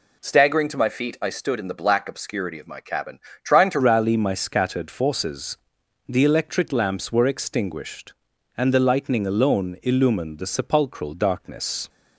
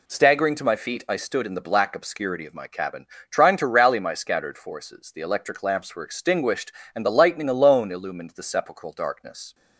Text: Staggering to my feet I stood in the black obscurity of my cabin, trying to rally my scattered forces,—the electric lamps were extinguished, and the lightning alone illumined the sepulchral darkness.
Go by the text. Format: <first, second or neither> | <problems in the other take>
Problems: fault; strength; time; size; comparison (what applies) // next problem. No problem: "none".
second | changes voice at "rally"; from 3.7 s on; 8.1 s long